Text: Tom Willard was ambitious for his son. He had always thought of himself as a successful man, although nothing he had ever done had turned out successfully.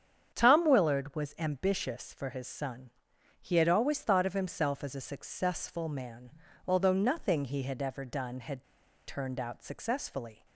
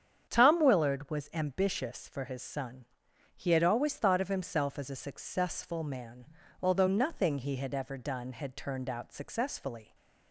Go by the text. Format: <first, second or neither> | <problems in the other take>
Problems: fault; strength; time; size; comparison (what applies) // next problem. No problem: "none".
second | starts louder than the rest; strong; until 1.3 s; 8 dB; strong in the second // pauses between "had" and "turned"; at 8.6 s; 0.43 s long